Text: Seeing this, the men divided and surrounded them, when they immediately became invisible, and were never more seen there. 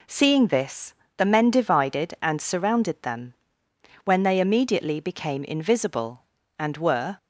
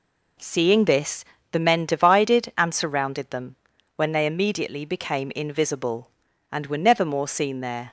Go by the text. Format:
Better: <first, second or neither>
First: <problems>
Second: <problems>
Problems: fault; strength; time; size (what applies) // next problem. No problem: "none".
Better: second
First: stops before "never more seen there"; at 7.1 s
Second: none